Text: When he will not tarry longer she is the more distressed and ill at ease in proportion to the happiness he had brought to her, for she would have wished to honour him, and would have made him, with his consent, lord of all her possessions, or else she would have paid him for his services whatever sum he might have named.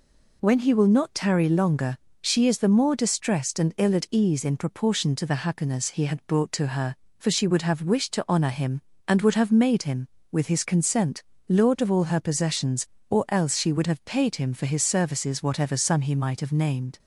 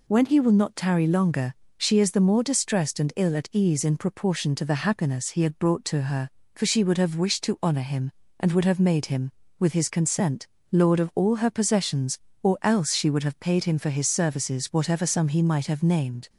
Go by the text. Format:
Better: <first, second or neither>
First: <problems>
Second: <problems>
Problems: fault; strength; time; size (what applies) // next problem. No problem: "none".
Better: neither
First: pauses between "longer" and "she"; slight; at 1.9 s; 0.24 s long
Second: pauses between "longer" and "she"; slight; at 1.5 s; 0.24 s long